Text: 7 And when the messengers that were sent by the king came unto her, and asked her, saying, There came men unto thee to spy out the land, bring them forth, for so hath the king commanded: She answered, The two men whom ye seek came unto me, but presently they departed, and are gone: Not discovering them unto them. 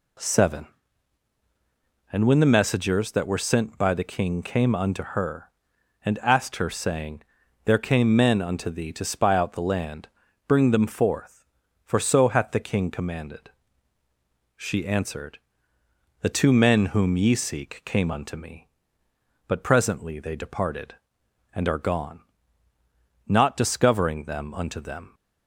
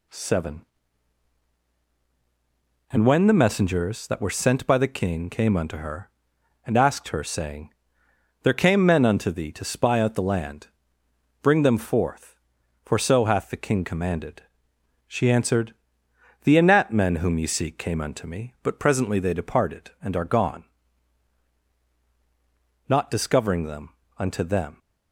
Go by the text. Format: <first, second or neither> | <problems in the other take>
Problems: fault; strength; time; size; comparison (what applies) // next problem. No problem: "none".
first | says "anat" for "two"; at 16.5 s // pauses between "them" and "unto"; slight; at 23.9 s; 0.28 s long